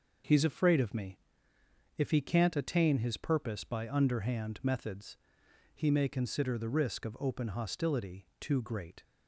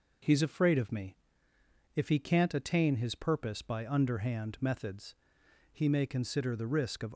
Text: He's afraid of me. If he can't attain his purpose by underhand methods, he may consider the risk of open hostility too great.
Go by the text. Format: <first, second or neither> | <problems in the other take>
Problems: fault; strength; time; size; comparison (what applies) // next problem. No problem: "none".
first | stops before "open hostility too great"; at 7.1 s